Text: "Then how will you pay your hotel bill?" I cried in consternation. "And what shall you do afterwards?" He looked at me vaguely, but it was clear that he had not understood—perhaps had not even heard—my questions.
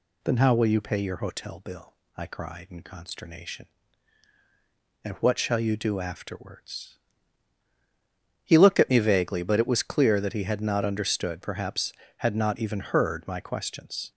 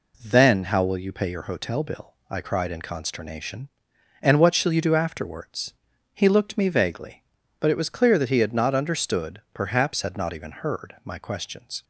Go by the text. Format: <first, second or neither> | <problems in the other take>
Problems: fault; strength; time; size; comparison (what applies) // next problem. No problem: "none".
first | skips "at"; at 6.5 s